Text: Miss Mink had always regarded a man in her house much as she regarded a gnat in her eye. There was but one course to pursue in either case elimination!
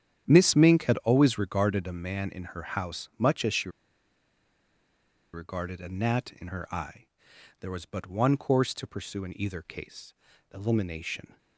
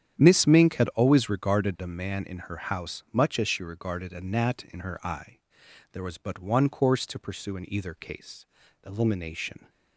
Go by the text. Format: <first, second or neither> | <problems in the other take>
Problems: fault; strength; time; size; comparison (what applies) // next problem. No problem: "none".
second | starts louder than the rest; strong; until 1.2 s; 9.5 dB; strong in the second // pauses between "she" and "regarded"; strong; at 3.6 s; 1.6 s long // pauses between "case" and "elimination"; at 10.1 s; 0.40 s long; also in the second